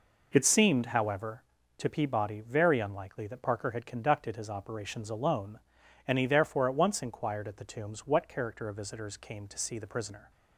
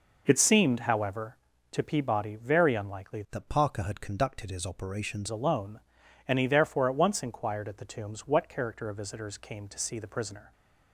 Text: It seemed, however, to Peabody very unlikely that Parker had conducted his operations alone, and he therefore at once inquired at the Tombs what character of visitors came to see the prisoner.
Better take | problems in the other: first | changes voice from "that" to "operations"; from 3.3 to 5.2 s; 1.9 s long

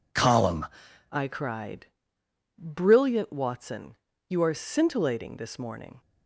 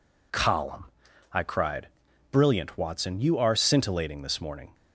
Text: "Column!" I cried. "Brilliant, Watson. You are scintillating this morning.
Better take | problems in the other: second | changes voice at "I"; from 1.1 s on; 4.9 s long

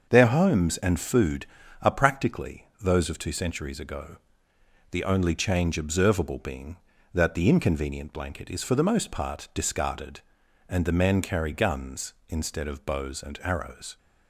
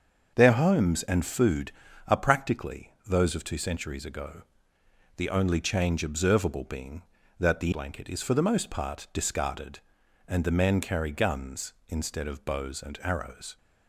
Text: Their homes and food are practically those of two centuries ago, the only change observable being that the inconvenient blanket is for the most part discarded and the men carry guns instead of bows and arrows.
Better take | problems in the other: first | starts louder than the rest; until 1.3 s; 6.5 dB; also in the first // skips "inconvenient"; at 7.7 s

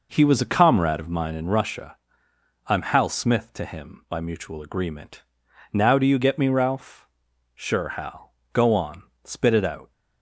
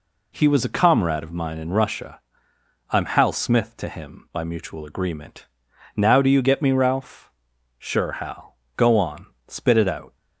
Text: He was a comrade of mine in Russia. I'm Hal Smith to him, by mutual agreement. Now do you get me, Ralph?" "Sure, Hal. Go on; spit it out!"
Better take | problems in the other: second | starts louder than the rest; noticeable; until 1.5 s; 5 dB

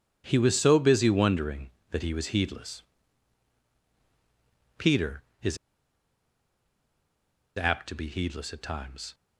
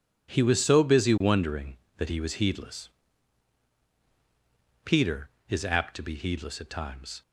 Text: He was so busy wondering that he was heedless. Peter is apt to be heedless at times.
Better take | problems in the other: second | pauses between "is" and "apt"; strong; at 5.5 s; 2.0 s long

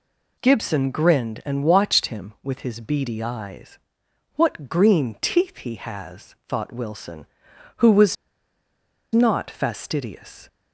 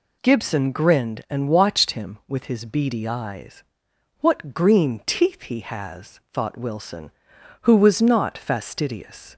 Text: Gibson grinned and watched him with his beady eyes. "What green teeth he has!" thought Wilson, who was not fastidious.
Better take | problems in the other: second | pauses between "was" and "not"; at 8.1 s; 0.98 s long

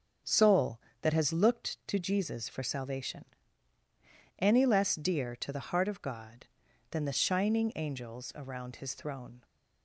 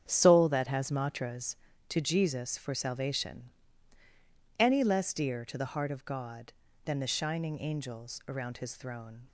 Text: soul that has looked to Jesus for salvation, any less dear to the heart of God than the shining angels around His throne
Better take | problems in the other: first | starts louder than the rest; strong; until 1.0 s; 8.5 dB; also in the first // says "matras" for "looked"; at 0.8 s

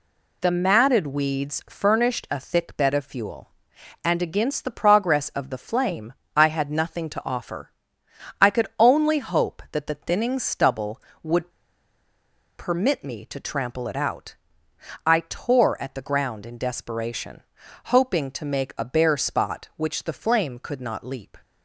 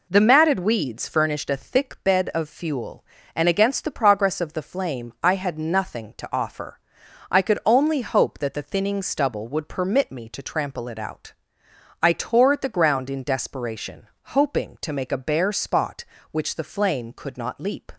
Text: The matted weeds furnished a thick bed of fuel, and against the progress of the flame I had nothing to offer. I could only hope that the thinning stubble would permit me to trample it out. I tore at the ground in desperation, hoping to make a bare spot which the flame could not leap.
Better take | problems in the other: second | pauses between "flame" and "I"; slight; at 6.1 s; 0.20 s long // pauses between "would" and "permit"; at 11.5 s; 1.0 s long

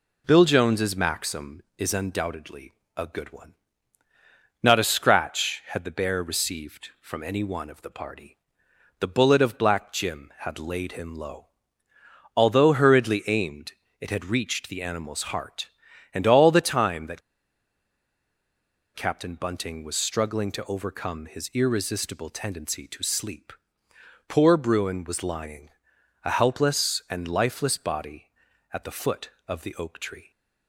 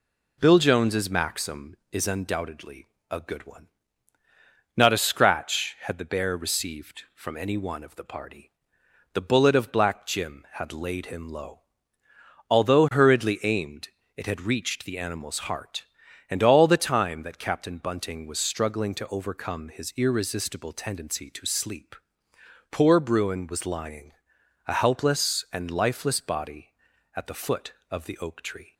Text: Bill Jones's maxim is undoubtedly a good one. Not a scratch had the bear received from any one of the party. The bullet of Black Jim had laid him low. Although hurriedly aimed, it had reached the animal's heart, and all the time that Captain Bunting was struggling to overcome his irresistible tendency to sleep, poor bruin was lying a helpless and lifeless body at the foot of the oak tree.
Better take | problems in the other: second | pauses between "undoubtedly" and "a"; slight; at 2.7 s; 0.26 s long; slight in the second // pauses between "that" and "Captain"; strong; at 17.2 s; 1.7 s long // pauses between "lying" and "a"; noticeable; at 25.6 s; 0.56 s long; noticeable in the second

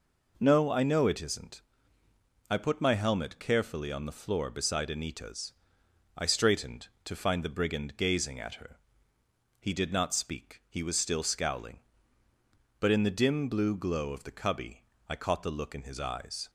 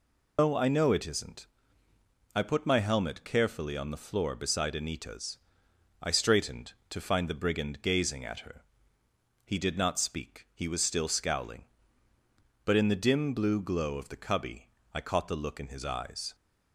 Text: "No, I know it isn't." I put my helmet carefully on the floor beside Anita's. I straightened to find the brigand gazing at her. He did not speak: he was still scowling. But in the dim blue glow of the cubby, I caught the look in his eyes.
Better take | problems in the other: first | loses the start of "No"; at 0.3 s; 170 ms

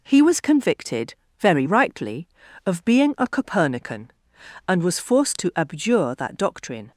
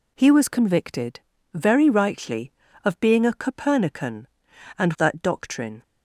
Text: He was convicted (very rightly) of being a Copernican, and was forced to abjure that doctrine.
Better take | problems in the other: first | skips "was forced to abjure"; at 4.9 s

